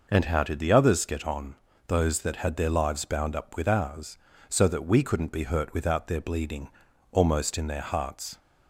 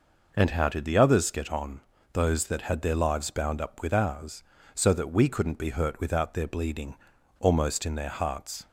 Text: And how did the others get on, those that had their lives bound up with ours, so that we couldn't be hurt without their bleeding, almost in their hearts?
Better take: neither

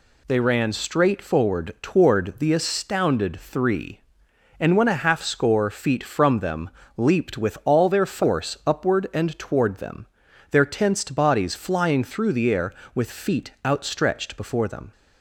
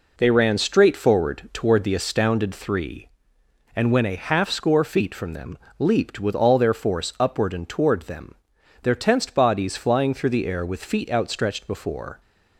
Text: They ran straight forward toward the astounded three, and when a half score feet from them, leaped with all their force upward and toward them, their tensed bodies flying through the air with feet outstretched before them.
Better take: first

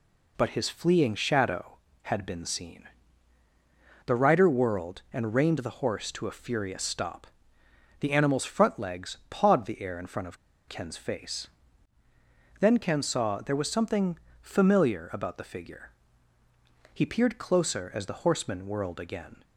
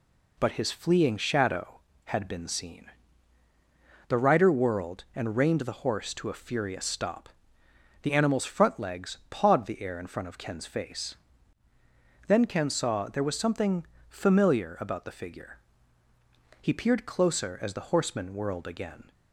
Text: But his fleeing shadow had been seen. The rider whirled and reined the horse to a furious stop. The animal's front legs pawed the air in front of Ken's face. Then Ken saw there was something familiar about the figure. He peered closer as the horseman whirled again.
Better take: second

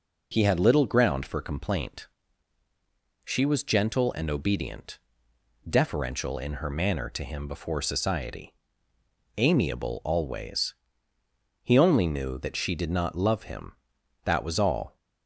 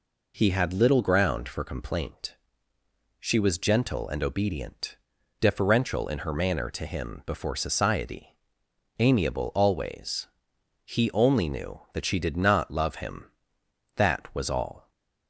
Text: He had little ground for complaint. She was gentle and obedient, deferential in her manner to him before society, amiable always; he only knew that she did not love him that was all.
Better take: neither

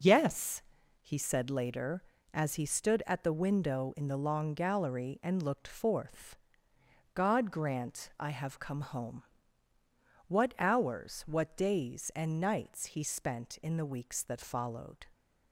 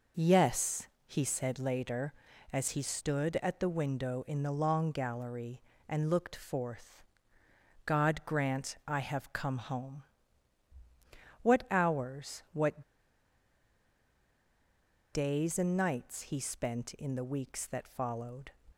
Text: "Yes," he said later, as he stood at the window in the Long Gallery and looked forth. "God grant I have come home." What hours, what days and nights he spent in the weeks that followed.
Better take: first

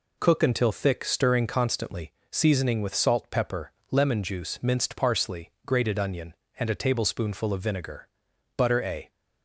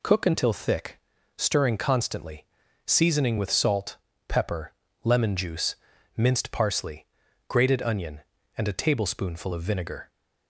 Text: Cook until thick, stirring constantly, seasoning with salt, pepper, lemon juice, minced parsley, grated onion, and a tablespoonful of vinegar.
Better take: second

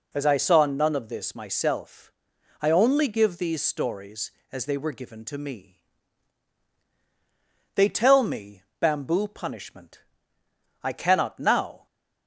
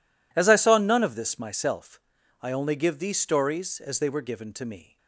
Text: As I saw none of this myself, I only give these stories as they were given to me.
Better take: second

